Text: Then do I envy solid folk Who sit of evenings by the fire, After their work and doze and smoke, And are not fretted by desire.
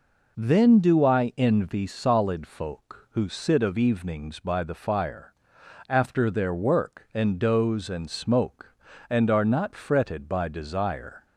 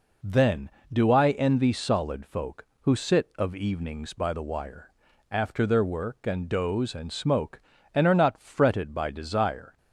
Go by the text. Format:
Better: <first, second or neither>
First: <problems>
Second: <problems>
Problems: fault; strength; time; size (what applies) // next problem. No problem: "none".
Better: first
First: none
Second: says "wire" for "fire"; at 4.4 s